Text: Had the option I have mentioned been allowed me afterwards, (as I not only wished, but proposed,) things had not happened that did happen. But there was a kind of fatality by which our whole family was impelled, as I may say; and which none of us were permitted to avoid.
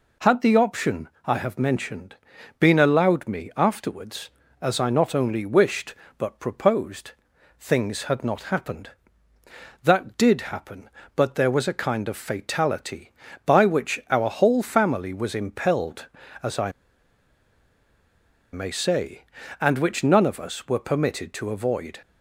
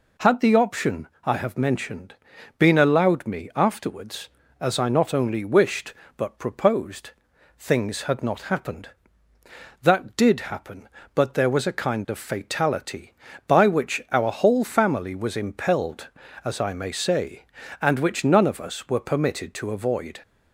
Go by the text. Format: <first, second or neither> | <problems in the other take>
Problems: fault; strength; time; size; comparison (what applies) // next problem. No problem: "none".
second | pauses between "option" and "I"; slight; at 1.0 s; 0.18 s long; slight in the second // pauses between "mentioned" and "been"; at 2.1 s; 0.42 s long; also in the second // pauses between "I" and "may"; strong; at 16.7 s; 1.8 s long